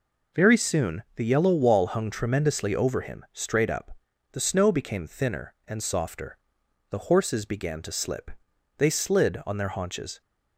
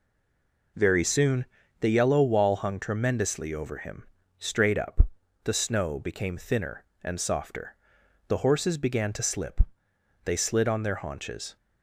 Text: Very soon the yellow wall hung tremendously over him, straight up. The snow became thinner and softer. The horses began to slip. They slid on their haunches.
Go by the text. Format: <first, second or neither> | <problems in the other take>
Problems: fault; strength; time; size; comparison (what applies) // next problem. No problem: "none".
first | stays silent before the first word; slight; until 0.7 s; 0.7 s long // pauses between "soon" and "the"; at 1.4 s; 0.38 s long